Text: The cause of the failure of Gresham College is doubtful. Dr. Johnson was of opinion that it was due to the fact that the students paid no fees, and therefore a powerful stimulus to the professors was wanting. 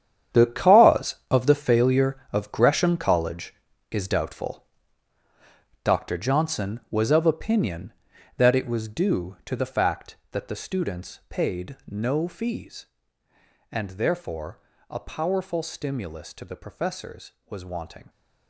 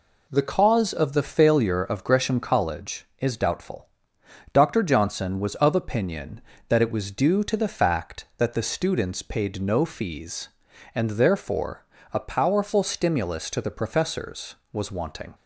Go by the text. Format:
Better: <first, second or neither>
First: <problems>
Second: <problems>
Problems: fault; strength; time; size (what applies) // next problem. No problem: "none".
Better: second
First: gets quieter; strong; throughout; 13 dB // pauses between "therefore" and "a"; slight; at 14.5 s; 0.28 s long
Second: pauses between "therefore" and "a"; slight; at 11.8 s; 0.28 s long